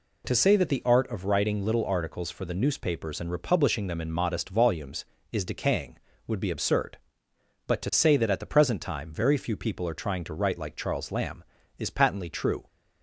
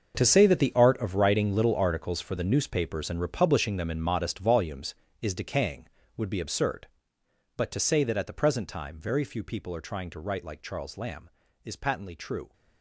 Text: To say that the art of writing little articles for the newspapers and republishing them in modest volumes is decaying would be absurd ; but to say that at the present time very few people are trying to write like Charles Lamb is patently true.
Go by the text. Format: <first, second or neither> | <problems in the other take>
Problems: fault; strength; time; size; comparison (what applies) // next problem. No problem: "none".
first | gets quieter; strong; throughout; 14.5 dB